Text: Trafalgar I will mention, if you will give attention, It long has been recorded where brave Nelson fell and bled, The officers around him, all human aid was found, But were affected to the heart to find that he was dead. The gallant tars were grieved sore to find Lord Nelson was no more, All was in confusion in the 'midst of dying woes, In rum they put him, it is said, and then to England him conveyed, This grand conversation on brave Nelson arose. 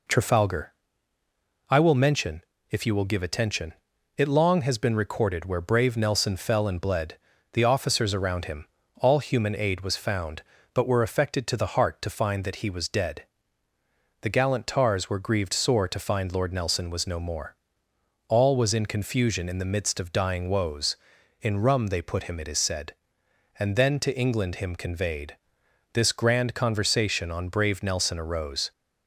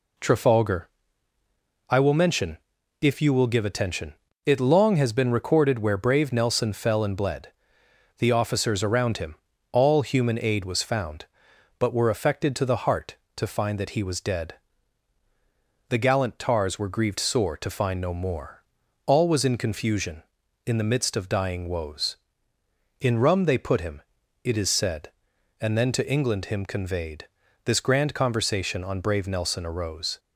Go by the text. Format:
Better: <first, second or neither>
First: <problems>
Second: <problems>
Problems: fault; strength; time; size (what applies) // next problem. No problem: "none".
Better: first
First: pauses between "Trafalgar" and "I"; noticeable; at 0.7 s; 0.98 s long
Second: pauses between "Trafalgar" and "I"; at 0.8 s; 1.0 s long // skips "Lord Nelson was"; at 18.0 s